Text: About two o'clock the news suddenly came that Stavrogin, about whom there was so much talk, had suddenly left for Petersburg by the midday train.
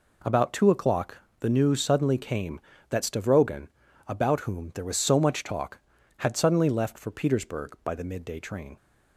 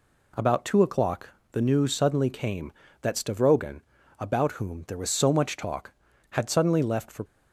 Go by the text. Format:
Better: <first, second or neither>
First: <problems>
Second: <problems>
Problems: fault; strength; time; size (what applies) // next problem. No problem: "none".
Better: first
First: pauses between "o'clock" and "the"; slight; at 1.1 s; 0.24 s long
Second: pauses between "o'clock" and "the"; slight; at 1.2 s; 0.24 s long // stops before "Petersburg by the midday train"; at 7.2 s